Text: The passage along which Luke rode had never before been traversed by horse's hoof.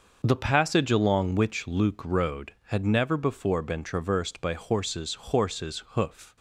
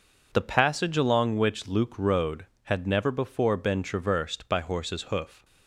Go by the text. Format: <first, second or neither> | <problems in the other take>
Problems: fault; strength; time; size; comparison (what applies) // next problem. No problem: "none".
second | starts louder than the rest; until 1.2 s; 6 dB // says "horse's" twice; at 5.1 s